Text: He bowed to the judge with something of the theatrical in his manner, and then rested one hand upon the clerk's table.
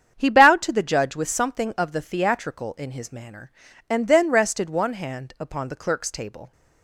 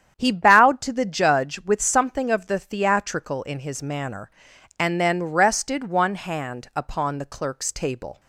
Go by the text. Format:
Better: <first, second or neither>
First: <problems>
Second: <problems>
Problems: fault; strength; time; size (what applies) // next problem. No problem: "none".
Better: neither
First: starts louder than the rest; strong; until 1.1 s; 8 dB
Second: starts louder than the rest; strong; until 1.1 s; 9 dB